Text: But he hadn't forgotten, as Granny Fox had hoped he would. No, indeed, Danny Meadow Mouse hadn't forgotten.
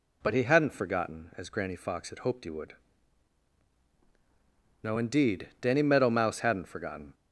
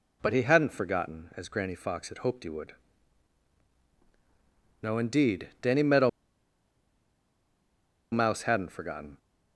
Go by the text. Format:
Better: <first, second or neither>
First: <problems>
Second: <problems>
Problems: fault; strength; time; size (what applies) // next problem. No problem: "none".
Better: first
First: none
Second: pauses between "Meadow" and "Mouse"; strong; at 6.0 s; 2.0 s long